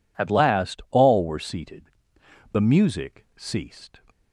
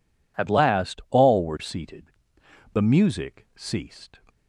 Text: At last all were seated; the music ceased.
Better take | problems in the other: neither | none

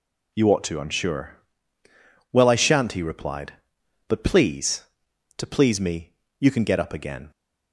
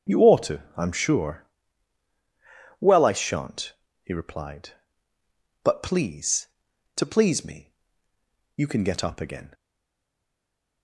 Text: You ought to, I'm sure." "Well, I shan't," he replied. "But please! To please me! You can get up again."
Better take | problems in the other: first | starts louder than the rest; strong; until 1.2 s; 7.5 dB // stays silent after the last word; noticeable; from 9.5 s on; 1.3 s long

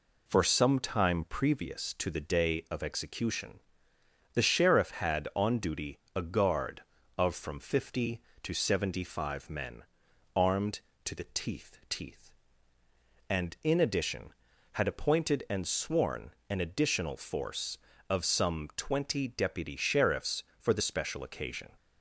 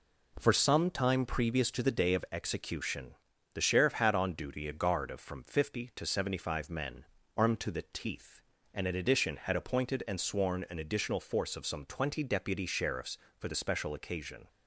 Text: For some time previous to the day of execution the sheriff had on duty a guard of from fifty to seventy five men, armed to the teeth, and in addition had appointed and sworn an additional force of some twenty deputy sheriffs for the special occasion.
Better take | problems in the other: second | pauses between "execution" and "the"; noticeable; at 3.5 s; 0.74 s long; also in the second // pauses between "duty" and "a"; slight; at 5.9 s; 0.16 s long // says "teeth" twice; at 11.8 s // pauses between "sworn" and "an"; slight; at 16.3 s; 0.18 s long

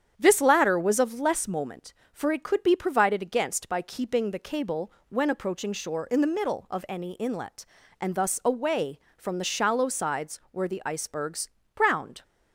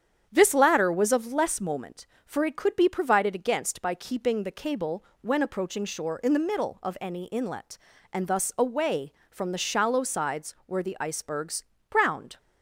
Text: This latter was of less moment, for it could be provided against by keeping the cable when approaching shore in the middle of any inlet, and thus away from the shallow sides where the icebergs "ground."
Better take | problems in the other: neither | starts louder than the rest; strong; the same in both // pauses between "cable" and "when"; slight; the same in both // pauses between "icebergs" and "ground"; slight; the same in both

